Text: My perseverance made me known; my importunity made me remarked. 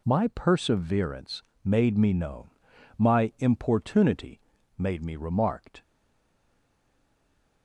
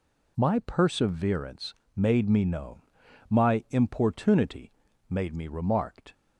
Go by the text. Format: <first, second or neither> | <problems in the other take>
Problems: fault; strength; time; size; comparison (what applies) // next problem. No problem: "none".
second | pauses between "perseverance" and "made"; slight; at 1.4 s; 0.20 s long; slight in the second // pauses between "importunity" and "made"; slight; at 4.4 s; 0.36 s long; slight in the second // stays silent after the last word; noticeable; from 5.8 s on; 1.8 s long